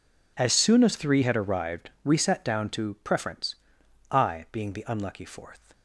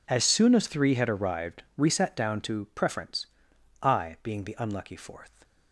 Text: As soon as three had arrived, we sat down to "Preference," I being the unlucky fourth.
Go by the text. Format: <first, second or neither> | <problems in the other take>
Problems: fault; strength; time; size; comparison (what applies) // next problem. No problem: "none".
neither | none